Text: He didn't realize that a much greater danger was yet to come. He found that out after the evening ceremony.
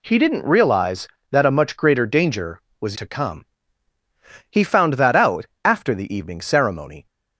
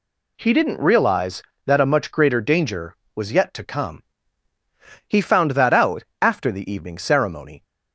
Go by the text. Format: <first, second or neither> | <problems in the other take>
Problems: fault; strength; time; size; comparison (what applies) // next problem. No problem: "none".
second | skips "yet"; at 2.9 s // pauses between "out" and "after"; slight; at 5.4 s; 0.18 s long; slight in the second